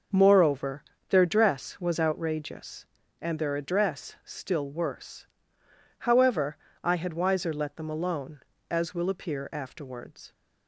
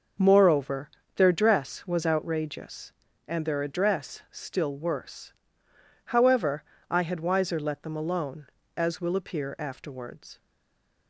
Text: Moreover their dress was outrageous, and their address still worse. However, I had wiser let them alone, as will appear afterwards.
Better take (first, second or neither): first